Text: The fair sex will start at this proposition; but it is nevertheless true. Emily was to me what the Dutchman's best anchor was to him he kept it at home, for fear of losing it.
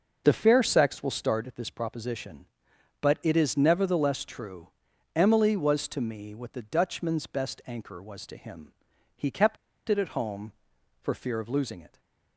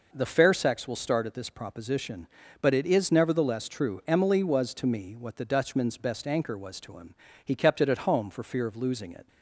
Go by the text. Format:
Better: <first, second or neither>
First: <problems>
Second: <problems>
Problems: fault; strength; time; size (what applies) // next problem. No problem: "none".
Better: second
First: pauses between "him" and "he"; at 8.7 s; 0.44 s long // pauses between "kept" and "it"; slight; at 9.5 s; 0.32 s long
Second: pauses between "him" and "he"; slight; at 7.1 s; 0.30 s long